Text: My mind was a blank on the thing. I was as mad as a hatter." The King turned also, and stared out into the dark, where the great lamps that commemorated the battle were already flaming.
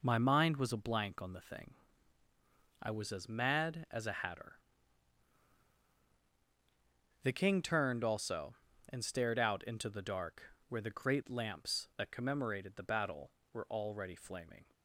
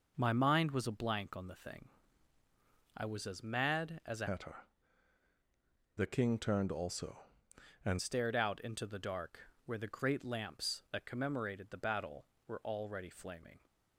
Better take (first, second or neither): first